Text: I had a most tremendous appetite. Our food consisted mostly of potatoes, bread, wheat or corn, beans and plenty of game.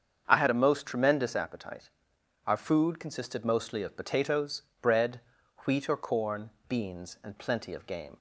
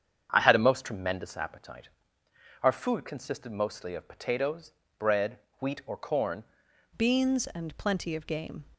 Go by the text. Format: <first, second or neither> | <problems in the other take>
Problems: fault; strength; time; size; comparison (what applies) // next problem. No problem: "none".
first | starts louder than the rest; strong; until 1.3 s; 8 dB; strong in the first // changes voice at "beans"; from 6.9 s on; 1.7 s long